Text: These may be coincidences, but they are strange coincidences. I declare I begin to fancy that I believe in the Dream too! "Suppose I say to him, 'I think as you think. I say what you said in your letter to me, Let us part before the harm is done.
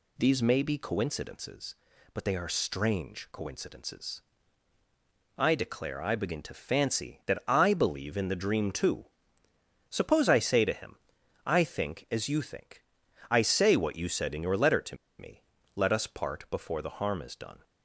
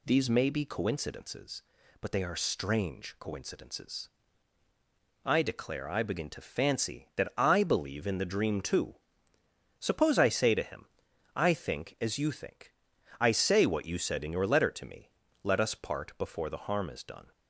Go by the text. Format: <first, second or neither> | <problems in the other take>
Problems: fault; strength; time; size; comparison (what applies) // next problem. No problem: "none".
second | pauses between "to" and "me"; slight; at 14.9 s; 0.23 s long